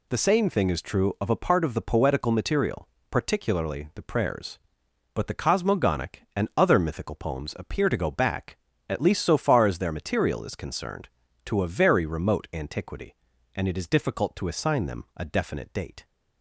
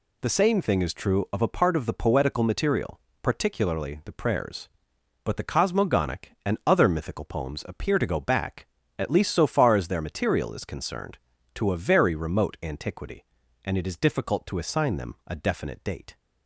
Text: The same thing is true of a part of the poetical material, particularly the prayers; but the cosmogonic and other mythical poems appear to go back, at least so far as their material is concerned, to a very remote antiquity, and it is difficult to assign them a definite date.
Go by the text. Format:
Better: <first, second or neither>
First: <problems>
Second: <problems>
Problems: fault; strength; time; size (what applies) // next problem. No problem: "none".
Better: neither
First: none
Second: none